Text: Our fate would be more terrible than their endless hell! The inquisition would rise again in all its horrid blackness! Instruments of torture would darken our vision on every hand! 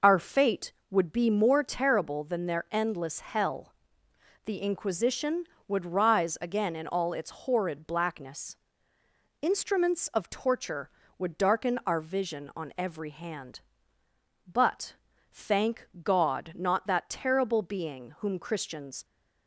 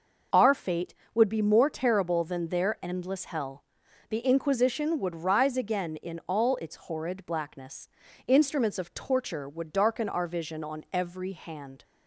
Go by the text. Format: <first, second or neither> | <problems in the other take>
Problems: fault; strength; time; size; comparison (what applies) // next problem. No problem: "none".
second | goes on to say "But thank God not that terrible being whom Christians"; strong; from 14.5 s on; 4.5 s long